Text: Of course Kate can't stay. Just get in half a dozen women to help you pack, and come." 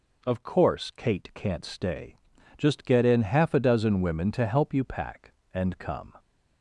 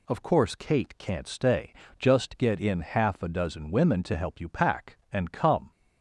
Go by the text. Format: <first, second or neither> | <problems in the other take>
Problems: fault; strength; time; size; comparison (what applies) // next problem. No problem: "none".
neither | none